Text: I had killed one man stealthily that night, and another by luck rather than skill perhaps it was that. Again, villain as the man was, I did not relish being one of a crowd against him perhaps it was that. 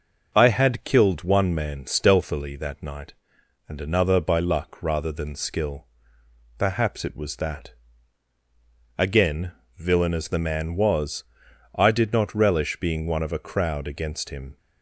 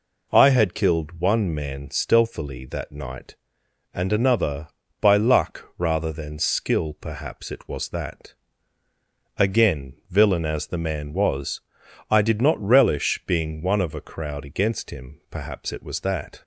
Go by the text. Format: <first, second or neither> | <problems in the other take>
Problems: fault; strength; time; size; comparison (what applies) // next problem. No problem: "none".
second | pauses between "skill" and "perhaps"; noticeable; at 5.8 s; 0.72 s long // stops before "perhaps it was that"; at 14.5 s